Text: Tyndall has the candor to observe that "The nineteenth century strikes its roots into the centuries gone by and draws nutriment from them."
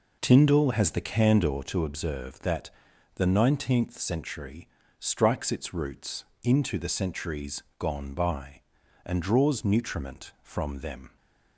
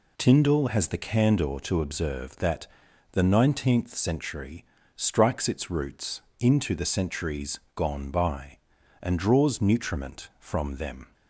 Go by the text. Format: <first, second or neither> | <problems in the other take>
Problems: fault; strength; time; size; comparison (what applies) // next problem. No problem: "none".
second | starts louder than the rest; noticeable; until 1.8 s; 4.5 dB // pauses between "that" and "The"; noticeable; at 2.7 s; 0.46 s long; noticeable in the second // pauses between "century" and "strikes"; slight; at 4.6 s; 0.32 s long; slight in the second // pauses between "roots" and "into"; slight; at 6.2 s; 0.18 s long; slight in the second // pauses between "centuries" and "gone"; slight; at 7.6 s; 0.16 s long; slight in the second